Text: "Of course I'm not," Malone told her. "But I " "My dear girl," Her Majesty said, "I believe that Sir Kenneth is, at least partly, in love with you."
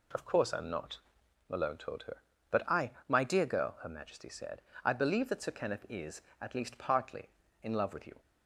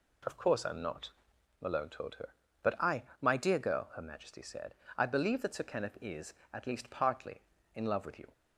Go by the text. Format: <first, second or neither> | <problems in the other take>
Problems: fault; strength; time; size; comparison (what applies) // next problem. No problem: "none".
neither | none